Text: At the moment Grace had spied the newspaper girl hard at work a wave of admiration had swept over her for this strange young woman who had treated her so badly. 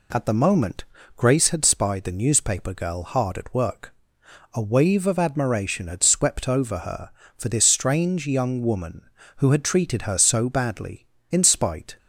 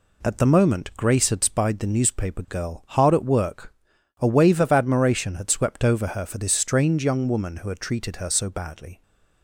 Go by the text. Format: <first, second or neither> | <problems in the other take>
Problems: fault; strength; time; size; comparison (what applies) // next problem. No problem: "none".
second | pauses between "moment" and "Grace"; slight; at 0.8 s; 0.32 s long // pauses between "work" and "a"; noticeable; at 3.9 s; 0.60 s long; noticeable in the second // goes on to say "In spite"; noticeable; from 11.2 s on; 0.68 s long